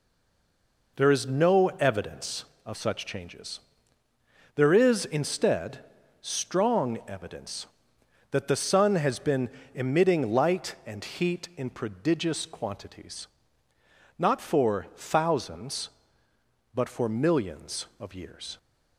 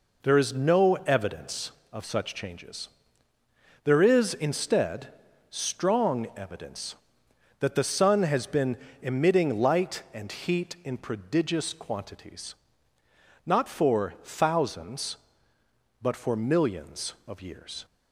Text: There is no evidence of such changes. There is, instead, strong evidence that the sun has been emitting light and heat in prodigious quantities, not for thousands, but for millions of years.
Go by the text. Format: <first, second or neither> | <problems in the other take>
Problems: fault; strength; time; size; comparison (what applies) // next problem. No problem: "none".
second | stays silent before the first word; slight; until 0.9 s; 0.9 s long // pauses between "been" and "emitting"; slight; at 9.4 s; 0.24 s long; slight in the second